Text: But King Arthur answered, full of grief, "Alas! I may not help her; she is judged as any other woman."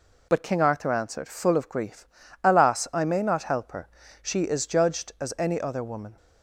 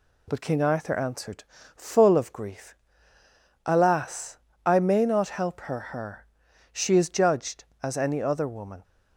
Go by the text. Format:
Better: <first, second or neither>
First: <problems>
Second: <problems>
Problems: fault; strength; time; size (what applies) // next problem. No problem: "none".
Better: first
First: none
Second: says "her" twice; at 5.7 s